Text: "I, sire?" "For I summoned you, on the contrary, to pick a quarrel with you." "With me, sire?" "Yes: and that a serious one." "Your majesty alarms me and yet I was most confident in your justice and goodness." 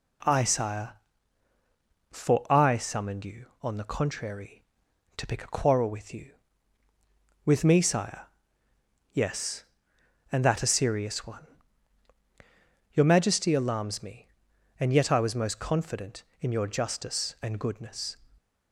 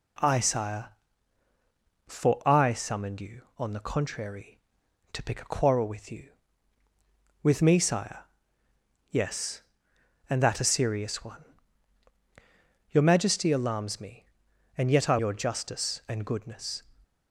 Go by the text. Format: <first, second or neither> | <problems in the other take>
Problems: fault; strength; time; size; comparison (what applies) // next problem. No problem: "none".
first | skips "was most confident in"; at 15.1 s